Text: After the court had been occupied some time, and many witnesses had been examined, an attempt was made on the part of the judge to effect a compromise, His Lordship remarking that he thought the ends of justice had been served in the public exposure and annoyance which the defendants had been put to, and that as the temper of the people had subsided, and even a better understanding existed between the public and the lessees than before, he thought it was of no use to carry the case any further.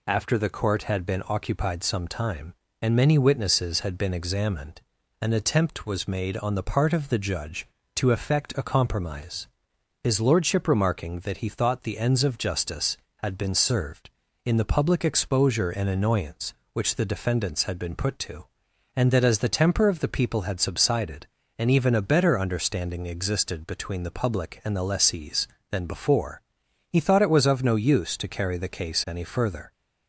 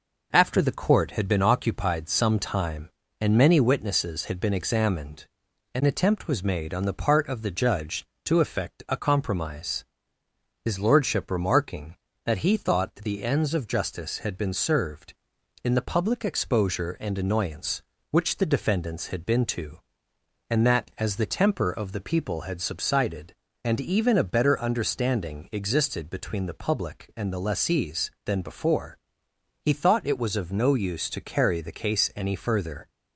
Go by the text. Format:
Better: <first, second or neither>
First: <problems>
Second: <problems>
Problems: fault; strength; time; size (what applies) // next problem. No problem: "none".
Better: first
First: none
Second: skips "put"; at 19.4 s